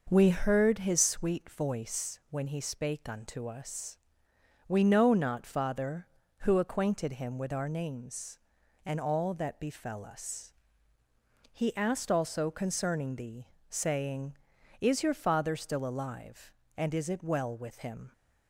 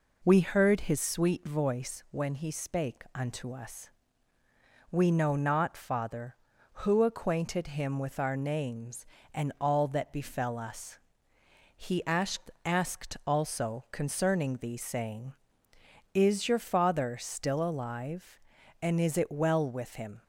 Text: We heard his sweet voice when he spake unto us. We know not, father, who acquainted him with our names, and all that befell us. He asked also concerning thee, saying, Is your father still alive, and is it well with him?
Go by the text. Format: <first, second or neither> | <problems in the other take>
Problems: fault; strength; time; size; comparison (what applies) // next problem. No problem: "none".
first | says "asked" twice; at 12.6 s